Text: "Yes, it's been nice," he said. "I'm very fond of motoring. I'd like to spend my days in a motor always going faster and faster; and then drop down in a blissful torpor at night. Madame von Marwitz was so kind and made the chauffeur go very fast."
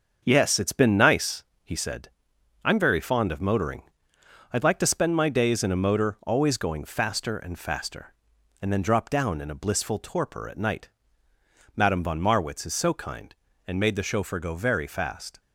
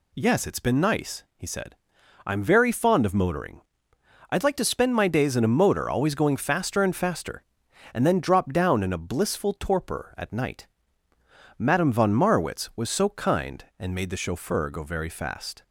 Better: second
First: starts louder than the rest; until 1.2 s; 7 dB // says "is" for "was"; at 12.6 s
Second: none

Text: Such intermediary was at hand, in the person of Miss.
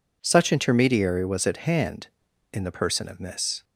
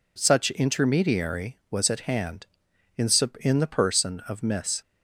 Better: first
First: none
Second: says "in" twice; at 3.4 s

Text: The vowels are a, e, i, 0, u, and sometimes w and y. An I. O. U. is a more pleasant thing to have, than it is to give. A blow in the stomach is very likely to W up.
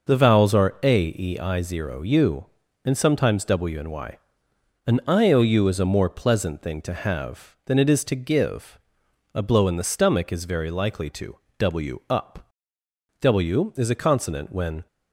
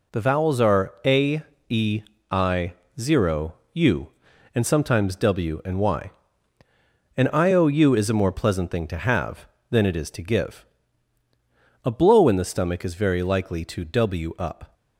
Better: second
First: pauses between "to" and "W"; slight; at 11.3 s; 0.24 s long // goes on to say "W is a consonant when"; strong; from 13.1 s on; 1.6 s long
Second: none

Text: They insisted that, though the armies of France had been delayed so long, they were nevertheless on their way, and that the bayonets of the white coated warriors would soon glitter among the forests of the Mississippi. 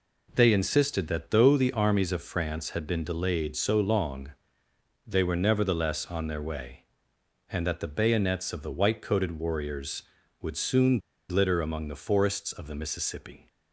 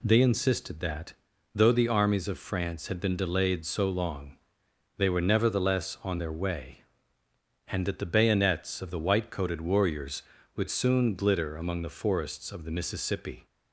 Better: second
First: pauses between "soon" and "glitter"; slight; at 10.9 s; 0.30 s long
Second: none

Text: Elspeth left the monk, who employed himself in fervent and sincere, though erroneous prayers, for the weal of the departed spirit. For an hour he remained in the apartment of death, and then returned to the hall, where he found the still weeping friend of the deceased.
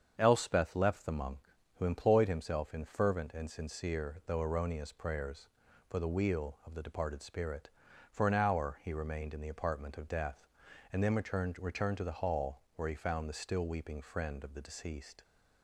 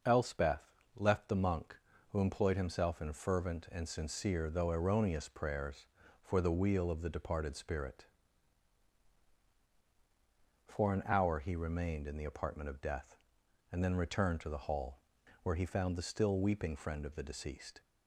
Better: second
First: starts louder than the rest; strong; until 1.1 s; 7.5 dB // says "returned" twice; at 11.5 s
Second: none

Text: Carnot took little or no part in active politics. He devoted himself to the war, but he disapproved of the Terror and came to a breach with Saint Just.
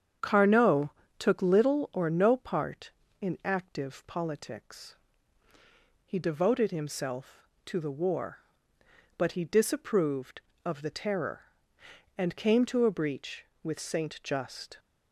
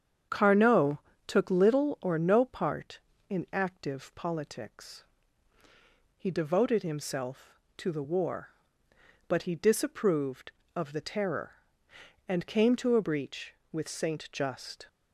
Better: neither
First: starts louder than the rest; strong; until 1.4 s; 8 dB // pauses between "Carnot" and "took"; slight; at 0.9 s; 0.28 s long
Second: starts louder than the rest; strong; until 1.5 s; 8 dB // pauses between "Carnot" and "took"; slight; at 0.9 s; 0.28 s long

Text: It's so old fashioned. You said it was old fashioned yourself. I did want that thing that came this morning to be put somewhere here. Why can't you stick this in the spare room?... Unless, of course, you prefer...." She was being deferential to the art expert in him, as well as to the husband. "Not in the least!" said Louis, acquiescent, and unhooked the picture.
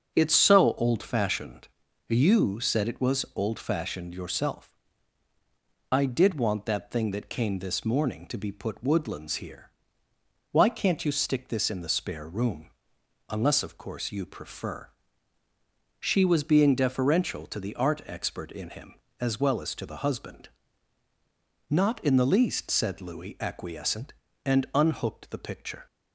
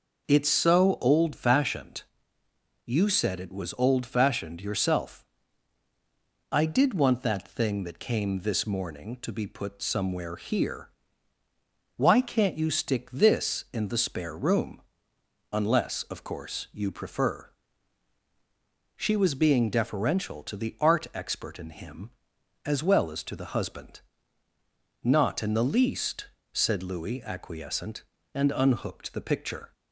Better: second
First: starts louder than the rest; until 1.1 s; 6.5 dB // says "woodlands" for "somewhere"; at 8.8 s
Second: none

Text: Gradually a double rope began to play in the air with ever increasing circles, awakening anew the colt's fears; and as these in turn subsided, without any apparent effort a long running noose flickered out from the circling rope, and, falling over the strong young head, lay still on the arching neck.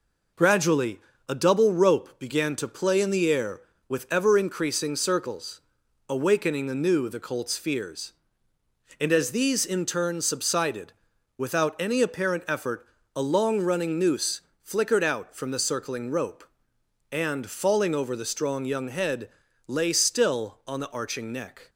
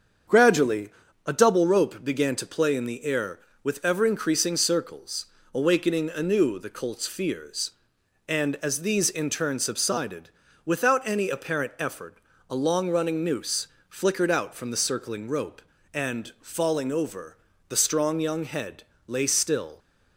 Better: first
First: pauses between "Gradually" and "a"; slight; at 0.9 s; 0.30 s long // pauses between "effort" and "a"; slight; at 12.8 s; 0.32 s long // pauses between "noose" and "flickered"; slight; at 14.4 s; 0.22 s long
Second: starts louder than the rest; until 1.6 s; 7 dB // pauses between "Gradually" and "a"; slight; at 0.9 s; 0.34 s long // pauses between "effort" and "a"; slight; at 12.1 s; 0.32 s long // pauses between "noose" and "flickered"; slight; at 13.6 s; 0.20 s long // pauses between "over" and "the"; slight; at 17.3 s; 0.30 s long // stops before "on the arching neck"; at 19.7 s

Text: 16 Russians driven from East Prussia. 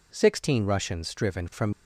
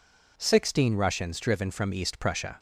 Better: second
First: stops before "East Prussia"; at 1.7 s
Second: none

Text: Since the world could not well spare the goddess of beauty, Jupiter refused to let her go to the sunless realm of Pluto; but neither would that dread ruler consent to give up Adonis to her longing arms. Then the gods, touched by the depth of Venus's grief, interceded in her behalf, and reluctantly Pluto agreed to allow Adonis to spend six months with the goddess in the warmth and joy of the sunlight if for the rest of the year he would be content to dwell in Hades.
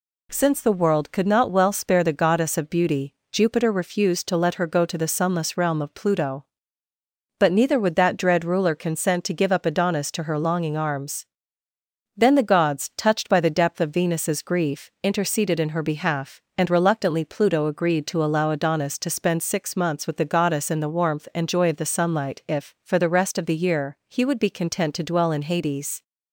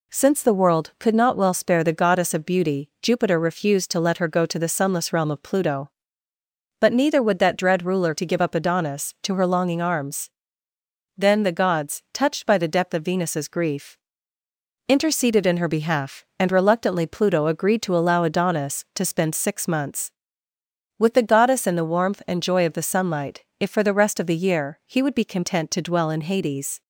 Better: first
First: none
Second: skips "consent"; at 8.1 s // pauses between "sunlight" and "if"; slight; at 23.4 s; 0.16 s long

